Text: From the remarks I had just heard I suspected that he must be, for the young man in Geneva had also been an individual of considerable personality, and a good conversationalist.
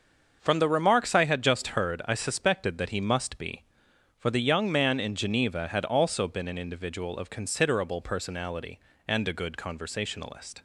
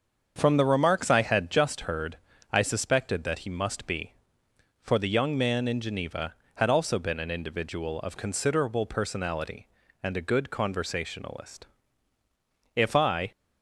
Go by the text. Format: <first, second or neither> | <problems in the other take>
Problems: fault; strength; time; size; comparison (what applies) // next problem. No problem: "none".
first | starts louder than the rest; until 1.3 s; 7 dB; also in the first // pauses between "heard" and "I"; slight; at 2.1 s; 0.34 s long // goes on to say "If I"; from 12.7 s on; 0.56 s long